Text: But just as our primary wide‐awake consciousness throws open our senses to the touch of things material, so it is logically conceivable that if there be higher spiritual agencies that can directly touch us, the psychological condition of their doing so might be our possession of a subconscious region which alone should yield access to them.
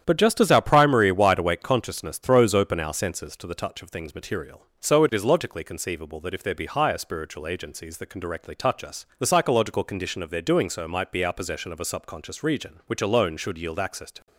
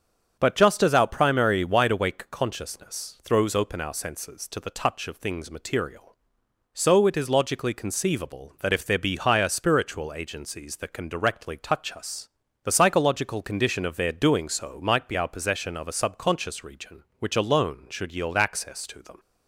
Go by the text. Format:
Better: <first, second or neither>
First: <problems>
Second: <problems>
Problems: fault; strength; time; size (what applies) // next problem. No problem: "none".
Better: second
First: starts louder than the rest; strong; until 1.0 s; 9.5 dB // stops before "them"; at 14.2 s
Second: starts louder than the rest; strong; until 1.3 s; 7 dB